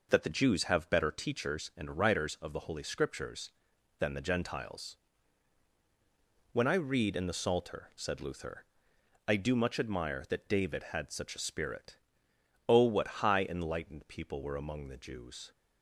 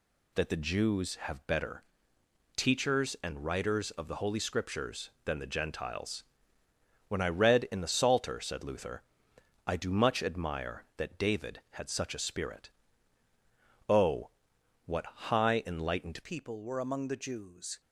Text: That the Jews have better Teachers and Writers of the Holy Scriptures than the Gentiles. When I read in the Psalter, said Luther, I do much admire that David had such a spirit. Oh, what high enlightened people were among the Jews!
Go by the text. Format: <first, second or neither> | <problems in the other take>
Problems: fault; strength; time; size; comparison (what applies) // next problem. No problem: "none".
first | pauses between "better" and "Teachers"; noticeable; at 1.8 s; 0.74 s long // changes voice at "people"; from 16.2 s on; 1.6 s long